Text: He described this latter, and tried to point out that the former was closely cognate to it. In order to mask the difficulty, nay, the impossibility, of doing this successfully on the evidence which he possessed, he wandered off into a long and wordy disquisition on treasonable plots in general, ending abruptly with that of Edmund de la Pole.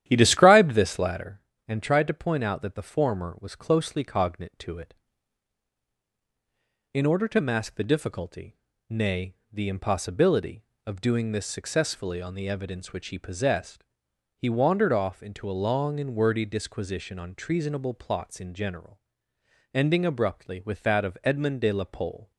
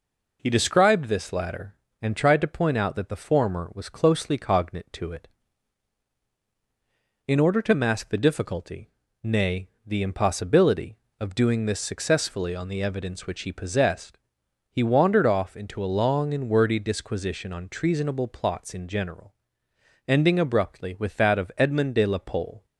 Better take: second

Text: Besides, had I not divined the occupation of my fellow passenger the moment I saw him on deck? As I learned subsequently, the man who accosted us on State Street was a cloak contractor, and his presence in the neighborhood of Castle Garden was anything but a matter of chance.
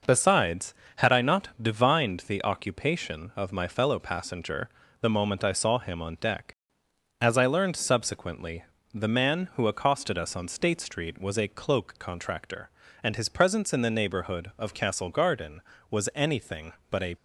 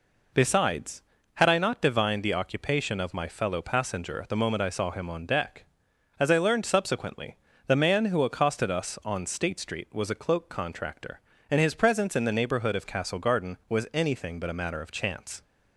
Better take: second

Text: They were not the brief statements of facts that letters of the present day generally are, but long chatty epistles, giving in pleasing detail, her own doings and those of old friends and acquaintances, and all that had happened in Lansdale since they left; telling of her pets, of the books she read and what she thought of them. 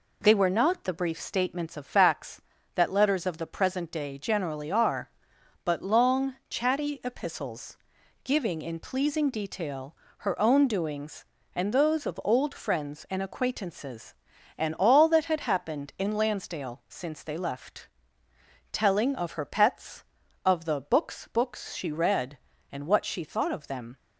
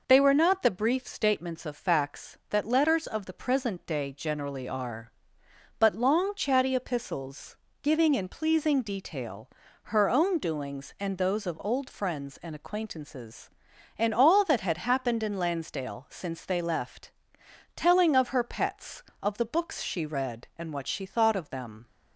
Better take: second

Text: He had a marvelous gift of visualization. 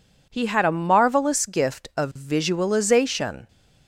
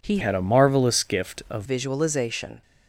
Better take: first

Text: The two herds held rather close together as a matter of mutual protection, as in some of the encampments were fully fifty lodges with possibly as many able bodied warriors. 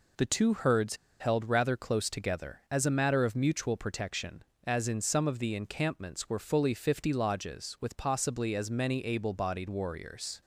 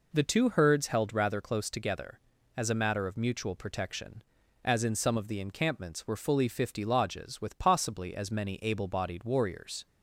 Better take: second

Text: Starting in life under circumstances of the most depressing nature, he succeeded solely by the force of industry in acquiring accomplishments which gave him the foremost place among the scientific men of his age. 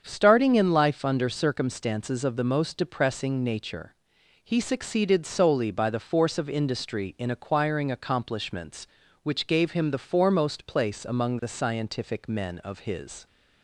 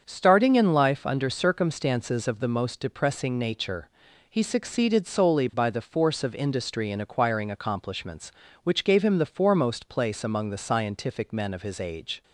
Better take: second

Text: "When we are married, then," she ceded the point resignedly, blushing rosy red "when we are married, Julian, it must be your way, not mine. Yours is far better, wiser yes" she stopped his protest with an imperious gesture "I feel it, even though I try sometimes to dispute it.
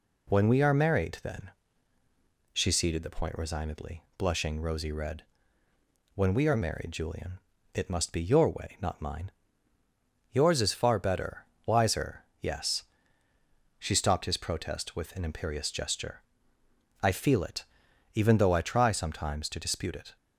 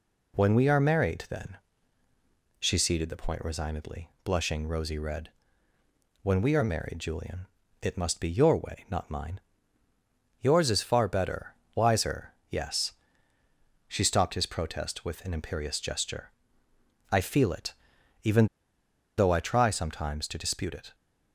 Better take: first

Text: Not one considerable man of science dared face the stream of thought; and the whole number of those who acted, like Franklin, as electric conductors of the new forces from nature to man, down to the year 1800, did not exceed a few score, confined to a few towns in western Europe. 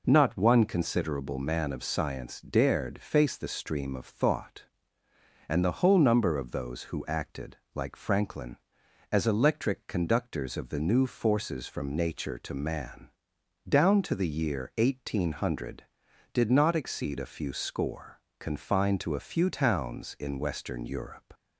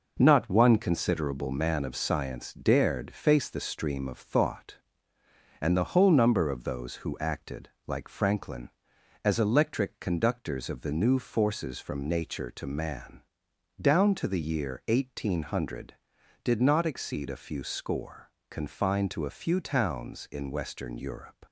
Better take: first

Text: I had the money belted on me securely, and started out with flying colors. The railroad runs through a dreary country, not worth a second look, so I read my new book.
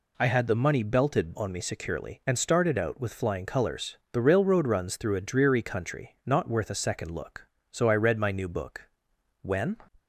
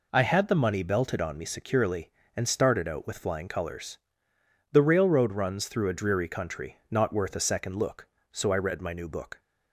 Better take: second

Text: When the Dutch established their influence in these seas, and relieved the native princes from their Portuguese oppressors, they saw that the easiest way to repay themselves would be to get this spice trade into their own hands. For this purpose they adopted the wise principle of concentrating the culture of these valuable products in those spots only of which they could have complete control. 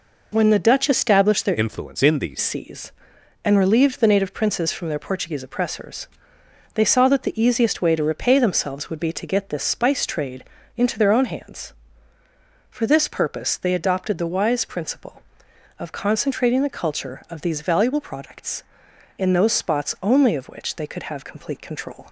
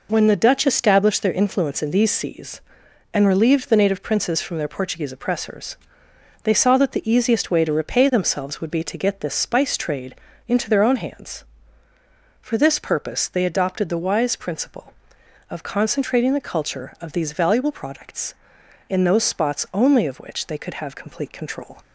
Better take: second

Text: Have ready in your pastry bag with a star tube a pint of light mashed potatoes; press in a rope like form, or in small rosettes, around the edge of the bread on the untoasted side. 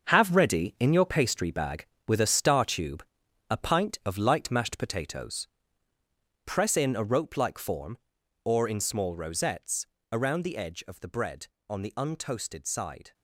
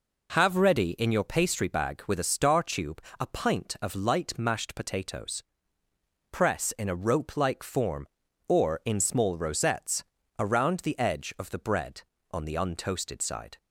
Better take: second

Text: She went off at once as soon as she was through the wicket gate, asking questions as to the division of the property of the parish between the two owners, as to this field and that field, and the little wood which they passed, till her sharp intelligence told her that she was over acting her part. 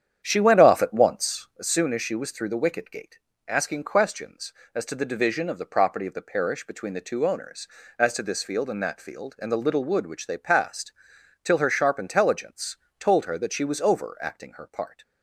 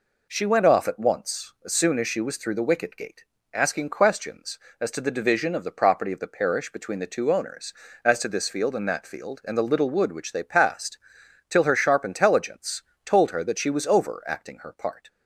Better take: second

